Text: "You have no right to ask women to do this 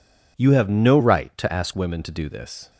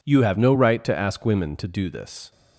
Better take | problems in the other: second | changes voice from "right" to "ask"; from 0.9 to 1.7 s; 0.8 s long

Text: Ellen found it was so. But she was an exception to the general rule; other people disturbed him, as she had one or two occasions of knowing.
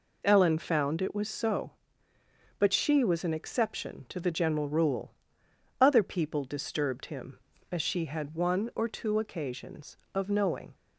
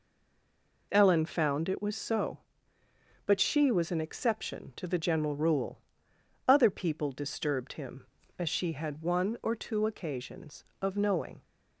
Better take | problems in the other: first | stays silent before the first word; slight; until 0.9 s; 0.9 s long

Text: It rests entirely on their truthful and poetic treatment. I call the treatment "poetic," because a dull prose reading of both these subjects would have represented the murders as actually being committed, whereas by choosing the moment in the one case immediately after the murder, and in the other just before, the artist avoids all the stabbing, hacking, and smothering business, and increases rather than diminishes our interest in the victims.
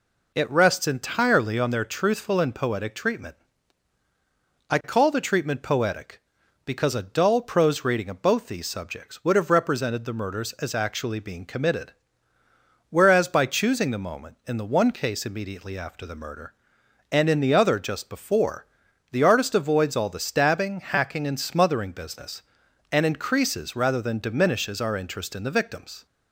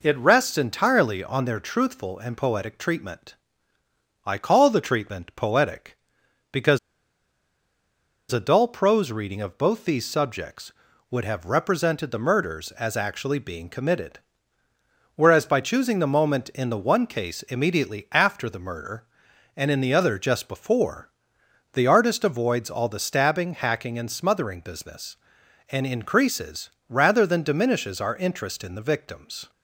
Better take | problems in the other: first | pauses between "because" and "a"; strong; at 6.7 s; 1.5 s long // pauses between "increases" and "rather"; slight; at 26.6 s; 0.18 s long

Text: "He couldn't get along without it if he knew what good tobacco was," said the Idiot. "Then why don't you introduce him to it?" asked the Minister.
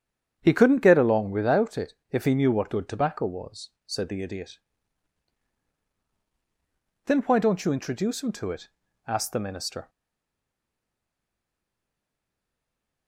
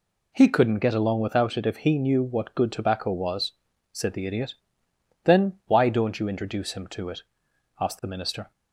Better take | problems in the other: second | starts louder than the rest; strong; until 1.4 s; 8.5 dB // pauses between "it" and "if"; slight; at 1.9 s; 0.16 s long // stays silent after the last word; strong; from 9.8 s on; 3.2 s long

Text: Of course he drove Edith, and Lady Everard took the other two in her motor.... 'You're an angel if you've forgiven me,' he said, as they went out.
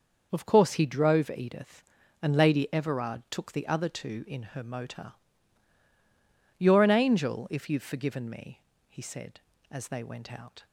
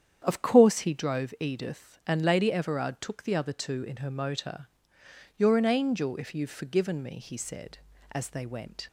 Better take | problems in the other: first | starts louder than the rest; strong; until 1.2 s; 8.5 dB; noticeable in the first // stops before "out"; at 8.8 s

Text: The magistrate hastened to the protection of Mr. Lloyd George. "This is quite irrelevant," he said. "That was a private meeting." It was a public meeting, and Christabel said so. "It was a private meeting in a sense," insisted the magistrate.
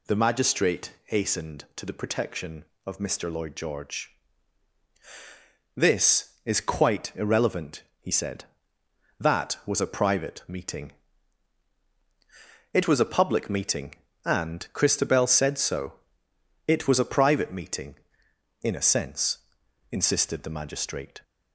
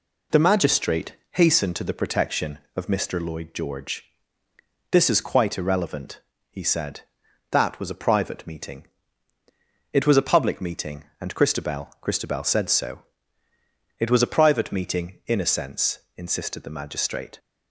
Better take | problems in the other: first | pauses between "magistrate" and "hastened"; slight; at 1.1 s; 0.16 s long // says "Christabel" twice; at 12.0 s

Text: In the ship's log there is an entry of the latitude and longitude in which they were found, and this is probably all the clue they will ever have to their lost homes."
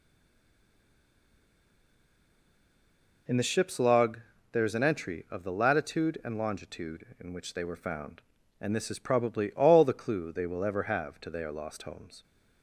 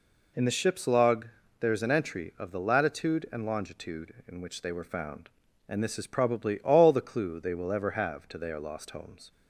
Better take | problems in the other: second | stays silent before the first word; strong; until 3.2 s; 3.2 s long // pauses between "log" and "there"; slight; at 4.2 s; 0.32 s long; slight in the second

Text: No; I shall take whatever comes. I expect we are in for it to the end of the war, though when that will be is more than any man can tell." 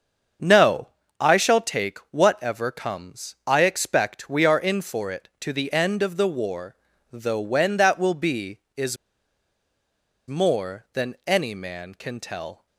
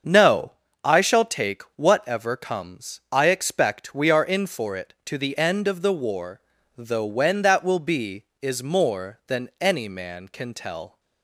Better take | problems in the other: second | starts louder than the rest; until 1.7 s; 7 dB; also in the second // pauses between "is" and "more"; strong; at 8.9 s; 1.3 s long

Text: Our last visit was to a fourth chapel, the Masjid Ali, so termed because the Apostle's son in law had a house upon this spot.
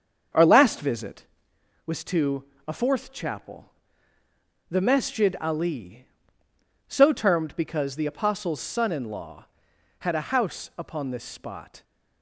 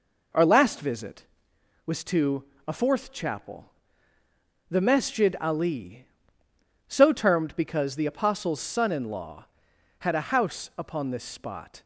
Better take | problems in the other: second | starts louder than the rest; until 1.3 s; 7 dB // pauses between "to" and "a"; slight; at 2.4 s; 0.22 s long; slight in the second

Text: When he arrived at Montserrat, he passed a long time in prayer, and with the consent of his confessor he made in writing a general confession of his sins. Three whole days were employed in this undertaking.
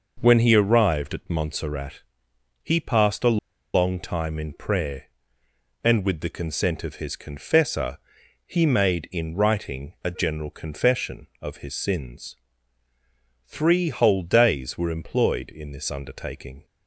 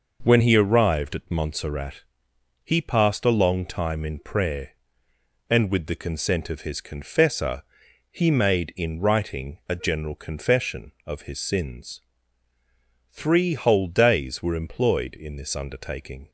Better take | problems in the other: second | pauses between "a" and "long"; at 3.3 s; 0.37 s long // pauses between "confessor" and "he"; noticeable; at 7.9 s; 0.48 s long; noticeable in the second

